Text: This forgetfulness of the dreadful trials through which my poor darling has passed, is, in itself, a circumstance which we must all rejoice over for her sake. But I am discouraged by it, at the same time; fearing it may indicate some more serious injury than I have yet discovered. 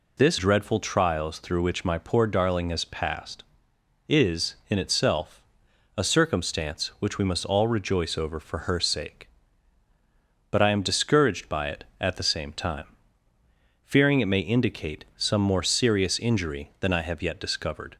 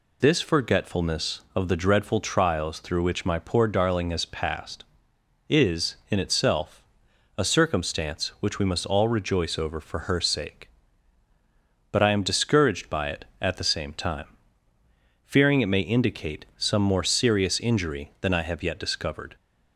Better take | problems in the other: second | skips "forgetfulness of the"; at 0.3 s

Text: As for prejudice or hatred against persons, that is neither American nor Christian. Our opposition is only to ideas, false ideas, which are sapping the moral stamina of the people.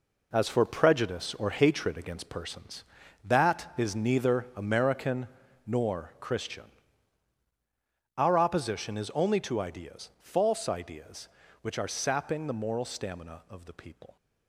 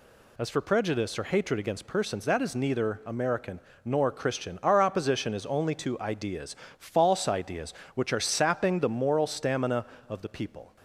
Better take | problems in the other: second | gets quieter; strong; throughout; 9 dB // pauses between "American" and "nor"; at 5.2 s; 0.38 s long; slight in the second

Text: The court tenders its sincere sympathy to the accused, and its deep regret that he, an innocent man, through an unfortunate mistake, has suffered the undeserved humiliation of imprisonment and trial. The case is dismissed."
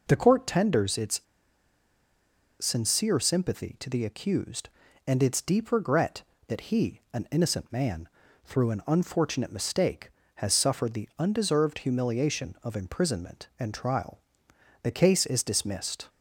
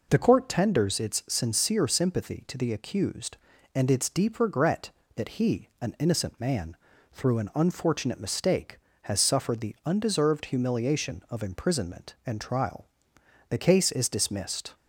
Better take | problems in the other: second | pauses between "its" and "sincere"; strong; at 1.2 s; 1.4 s long

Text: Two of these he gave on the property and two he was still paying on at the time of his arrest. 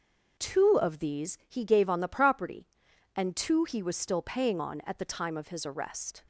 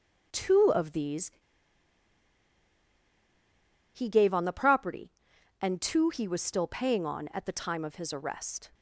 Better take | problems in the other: first | pauses between "these" and "he"; strong; at 1.3 s; 2.6 s long

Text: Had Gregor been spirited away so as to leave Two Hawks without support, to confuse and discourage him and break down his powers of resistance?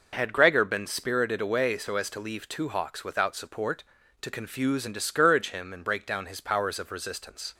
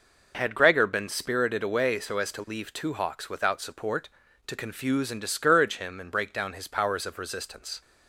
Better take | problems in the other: neither | none

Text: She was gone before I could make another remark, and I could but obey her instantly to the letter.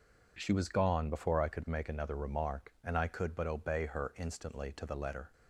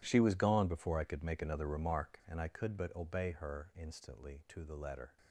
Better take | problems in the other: first | gets quieter; strong; throughout; 17 dB

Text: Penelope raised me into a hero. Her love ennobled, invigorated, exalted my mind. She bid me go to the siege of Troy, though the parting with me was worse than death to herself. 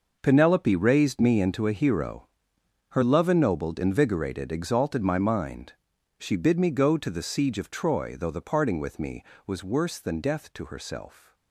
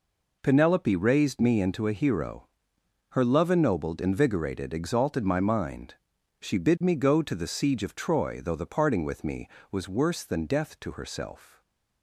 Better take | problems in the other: second | gets quieter; strong; throughout; 13 dB

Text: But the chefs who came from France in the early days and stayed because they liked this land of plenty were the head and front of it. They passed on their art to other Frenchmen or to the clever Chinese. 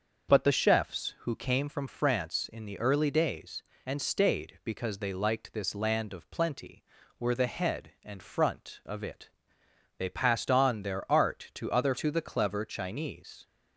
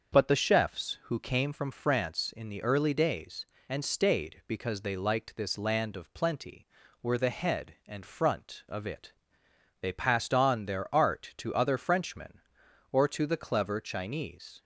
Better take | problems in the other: second | starts louder than the rest; until 1.3 s; 6.5 dB; also in the second // skips "Frenchmen or"; at 11.9 s

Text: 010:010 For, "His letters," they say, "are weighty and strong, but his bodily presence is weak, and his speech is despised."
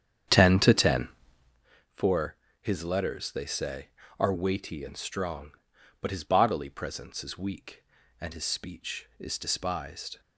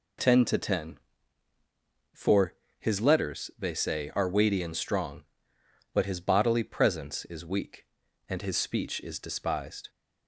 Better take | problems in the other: second | starts louder than the rest; strong; until 1.7 s; 9 dB

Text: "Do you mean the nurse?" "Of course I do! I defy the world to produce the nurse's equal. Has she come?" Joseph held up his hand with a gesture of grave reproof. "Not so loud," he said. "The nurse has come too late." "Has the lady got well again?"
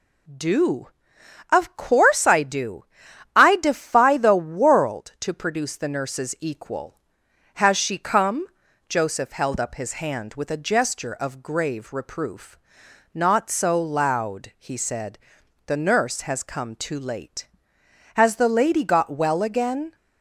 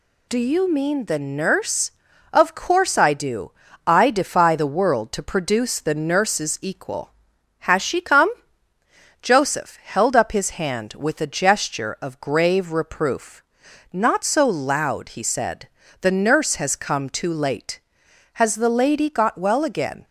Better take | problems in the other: second | skips "you mean the nurse"; at 1.1 s

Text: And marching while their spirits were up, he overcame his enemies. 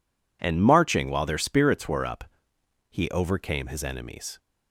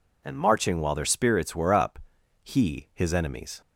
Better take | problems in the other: first | skips "overcame"; at 2.8 s

